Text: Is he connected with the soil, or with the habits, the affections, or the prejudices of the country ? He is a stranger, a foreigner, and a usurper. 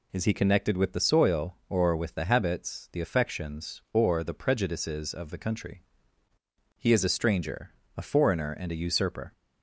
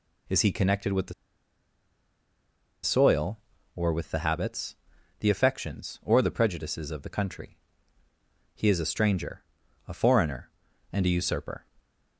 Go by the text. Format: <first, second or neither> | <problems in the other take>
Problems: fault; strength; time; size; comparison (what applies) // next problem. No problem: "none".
first | pauses between "the" and "soil"; strong; at 1.1 s; 1.6 s long